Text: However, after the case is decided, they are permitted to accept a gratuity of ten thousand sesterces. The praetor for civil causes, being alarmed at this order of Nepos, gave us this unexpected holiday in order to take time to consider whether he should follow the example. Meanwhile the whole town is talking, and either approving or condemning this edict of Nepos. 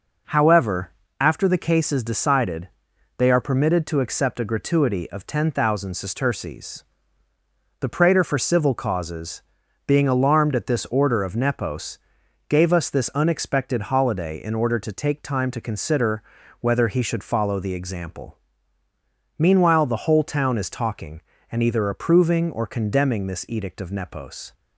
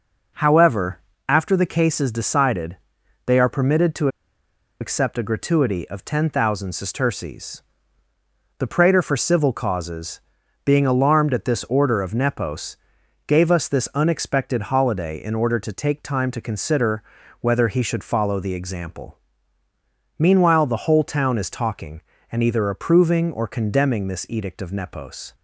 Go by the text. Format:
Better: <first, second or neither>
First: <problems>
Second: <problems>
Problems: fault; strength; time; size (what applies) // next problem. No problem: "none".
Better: first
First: pauses between "consider" and "whether"; at 16.2 s; 0.38 s long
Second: pauses between "to" and "accept"; noticeable; at 4.0 s; 0.72 s long // pauses between "consider" and "whether"; at 17.0 s; 0.38 s long